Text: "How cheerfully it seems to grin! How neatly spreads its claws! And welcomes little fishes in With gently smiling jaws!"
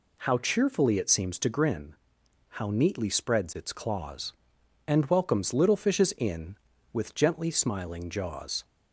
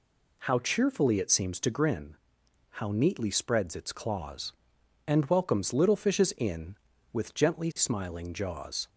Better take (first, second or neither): neither